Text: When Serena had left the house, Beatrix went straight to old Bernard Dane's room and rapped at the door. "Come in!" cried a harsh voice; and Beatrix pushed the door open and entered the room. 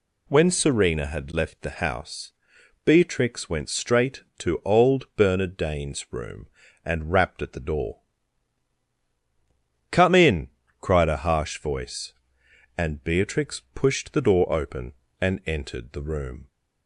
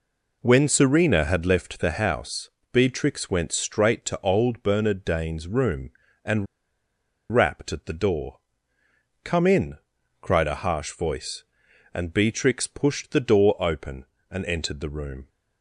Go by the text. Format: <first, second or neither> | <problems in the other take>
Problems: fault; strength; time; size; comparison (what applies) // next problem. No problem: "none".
first | pauses between "and" and "rapped"; noticeable; at 6.4 s; 0.86 s long